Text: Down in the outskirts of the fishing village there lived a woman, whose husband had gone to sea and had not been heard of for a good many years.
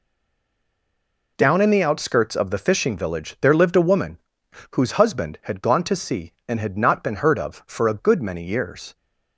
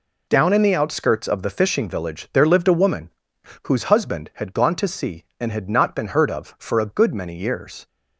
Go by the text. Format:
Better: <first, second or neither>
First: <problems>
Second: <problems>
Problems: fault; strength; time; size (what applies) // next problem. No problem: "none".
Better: second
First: stays silent before the first word; noticeable; until 1.3 s; 1.3 s long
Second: none